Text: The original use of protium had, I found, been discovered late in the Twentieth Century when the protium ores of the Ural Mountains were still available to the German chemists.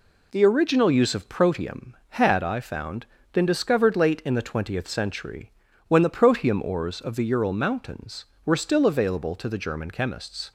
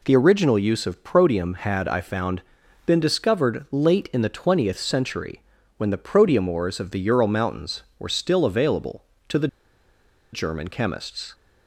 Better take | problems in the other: first | pauses between "Century" and "when"; slight; at 5.4 s; 0.36 s long; slight in the first // pauses between "the" and "German"; noticeable; at 9.4 s; 0.85 s long

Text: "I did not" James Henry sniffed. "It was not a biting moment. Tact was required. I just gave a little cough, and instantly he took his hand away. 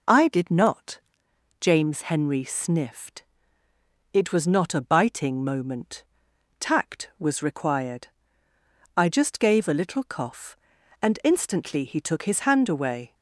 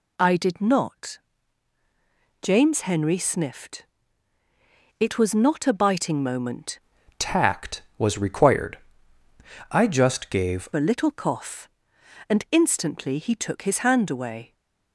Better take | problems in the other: first | pauses between "not" and "James"; at 1.1 s; 1.2 s long; noticeable in the first // changes voice from "Tact" to "gave"; from 7.1 to 10.6 s; 3.5 s long

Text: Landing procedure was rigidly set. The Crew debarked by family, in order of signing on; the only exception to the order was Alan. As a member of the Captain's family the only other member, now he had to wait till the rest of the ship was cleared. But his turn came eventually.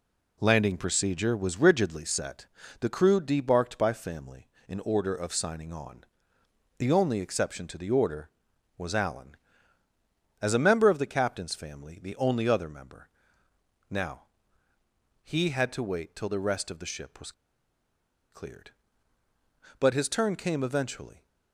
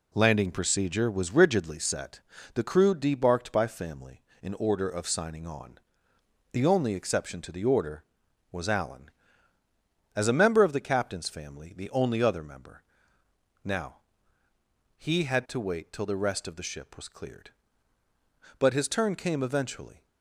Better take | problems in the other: second | pauses between "now" and "he"; noticeable; at 14.2 s; 0.98 s long; noticeable in the second // pauses between "was" and "cleared"; at 17.3 s; 1.0 s long

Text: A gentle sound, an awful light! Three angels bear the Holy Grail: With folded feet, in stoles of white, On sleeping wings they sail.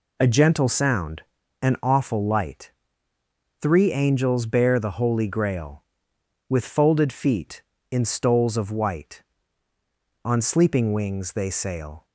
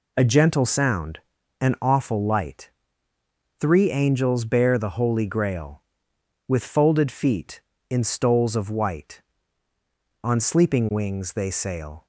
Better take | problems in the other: neither | none

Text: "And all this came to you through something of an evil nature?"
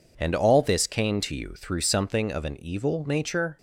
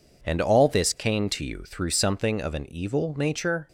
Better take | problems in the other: neither | none

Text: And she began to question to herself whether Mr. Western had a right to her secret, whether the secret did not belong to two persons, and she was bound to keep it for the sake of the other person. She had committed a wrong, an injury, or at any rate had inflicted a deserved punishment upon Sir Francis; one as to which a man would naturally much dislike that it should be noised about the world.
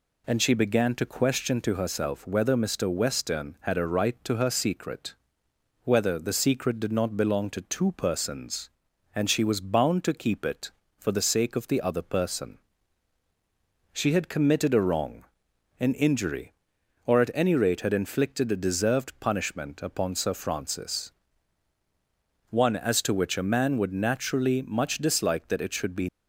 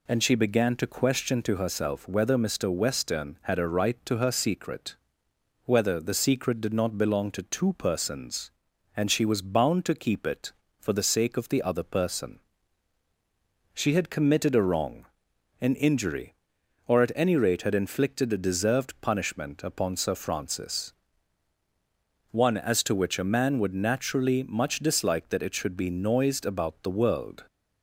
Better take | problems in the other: second | stops before "noised about the world"; at 26.0 s

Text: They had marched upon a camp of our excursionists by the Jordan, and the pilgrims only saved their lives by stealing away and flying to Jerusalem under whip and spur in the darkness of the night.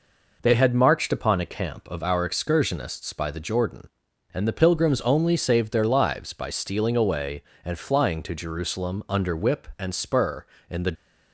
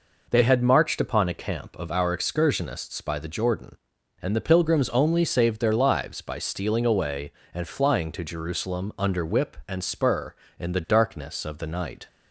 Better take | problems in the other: second | stops before "darkness of the night"; at 10.9 s

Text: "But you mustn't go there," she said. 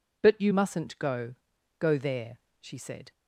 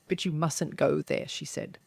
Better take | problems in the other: second | says "go" twice; at 1.7 s

